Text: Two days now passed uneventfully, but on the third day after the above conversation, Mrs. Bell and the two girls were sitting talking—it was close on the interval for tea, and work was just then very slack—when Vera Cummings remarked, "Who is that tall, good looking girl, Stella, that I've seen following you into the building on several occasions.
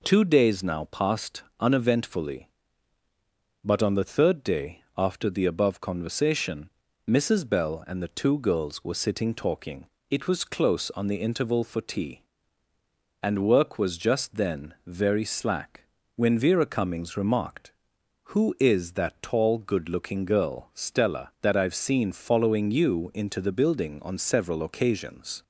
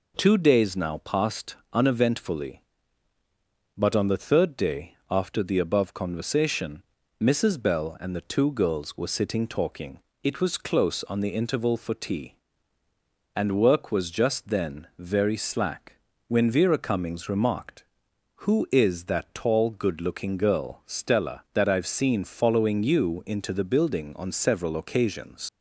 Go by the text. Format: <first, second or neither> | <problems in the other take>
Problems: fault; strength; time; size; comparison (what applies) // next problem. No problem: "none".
first | pauses between "passed" and "uneventfully"; slight; at 1.5 s; 0.18 s long; slight in the first // pauses between "day" and "after"; slight; at 4.9 s; 0.16 s long; slight in the first // leaves "occasions" unfinished; at 25.4 s; 75 ms